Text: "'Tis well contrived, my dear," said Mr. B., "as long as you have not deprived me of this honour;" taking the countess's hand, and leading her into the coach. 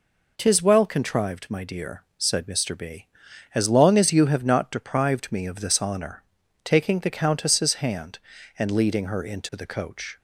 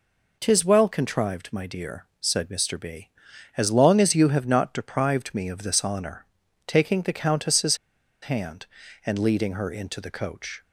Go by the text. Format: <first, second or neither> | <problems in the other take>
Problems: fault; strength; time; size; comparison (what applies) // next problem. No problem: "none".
first | pauses between "countess's" and "hand"; noticeable; at 7.7 s; 0.46 s long